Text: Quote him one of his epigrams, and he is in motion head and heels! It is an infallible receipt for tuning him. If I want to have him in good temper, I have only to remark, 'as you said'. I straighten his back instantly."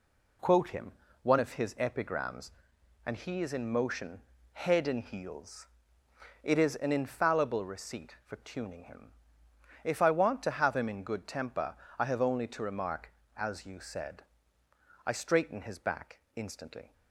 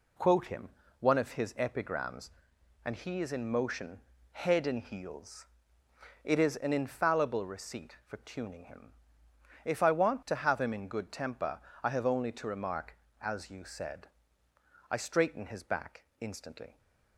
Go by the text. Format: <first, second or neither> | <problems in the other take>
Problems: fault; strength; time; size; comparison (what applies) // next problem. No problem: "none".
neither | pauses between "him" and "one"; slight; the same in both // pauses between "motion" and "head"; slight; the same in both